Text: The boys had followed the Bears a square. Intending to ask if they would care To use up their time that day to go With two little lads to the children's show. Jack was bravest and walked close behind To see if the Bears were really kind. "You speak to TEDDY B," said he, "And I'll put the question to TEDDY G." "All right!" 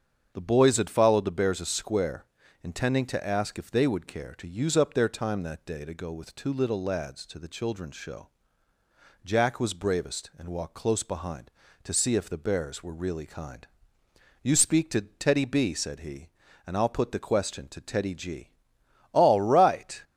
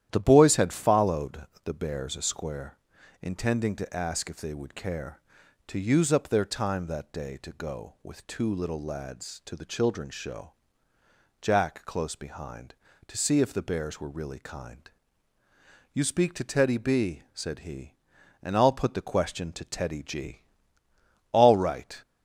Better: first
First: starts louder than the rest; strong; until 1.3 s; 7.5 dB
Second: starts louder than the rest; strong; until 1.1 s; 11.5 dB // pauses between "followed" and "the"; slight; at 1.4 s; 0.20 s long // skips "was bravest and walked"; at 11.8 s

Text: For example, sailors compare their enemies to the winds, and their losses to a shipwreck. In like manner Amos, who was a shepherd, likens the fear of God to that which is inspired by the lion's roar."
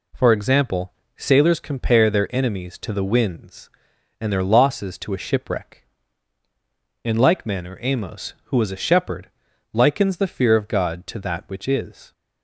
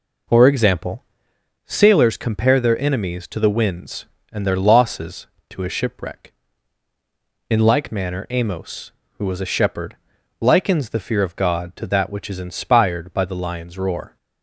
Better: second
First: stops before "inspired by the lion's roar"; at 12.1 s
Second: none

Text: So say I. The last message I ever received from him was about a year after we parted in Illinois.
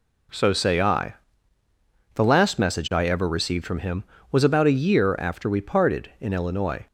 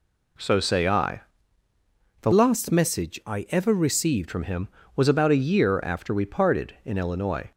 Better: first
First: none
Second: changes voice from "last" to "received"; from 2.3 to 4.2 s; 1.9 s long

